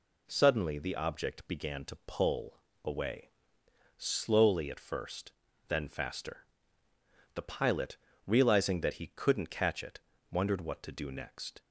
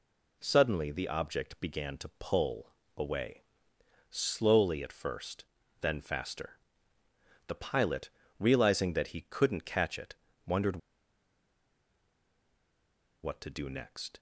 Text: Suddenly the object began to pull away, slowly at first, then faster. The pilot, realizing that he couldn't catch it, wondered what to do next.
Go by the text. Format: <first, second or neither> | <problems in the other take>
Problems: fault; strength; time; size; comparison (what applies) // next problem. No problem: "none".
first | pauses between "pull" and "away"; slight; at 2.7 s; 0.24 s long; slight in the first // pauses between "wondered" and "what"; strong; at 10.7 s; 2.4 s long